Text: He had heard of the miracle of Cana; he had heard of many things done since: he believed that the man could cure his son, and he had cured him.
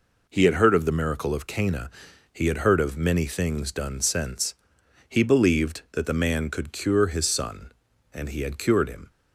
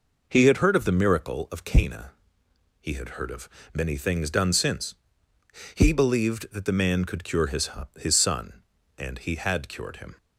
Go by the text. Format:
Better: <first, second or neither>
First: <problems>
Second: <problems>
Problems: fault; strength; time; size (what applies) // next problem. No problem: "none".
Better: first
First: none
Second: pauses between "of" and "many"; slight; at 3.4 s; 0.24 s long // says "his" twice; at 7.9 s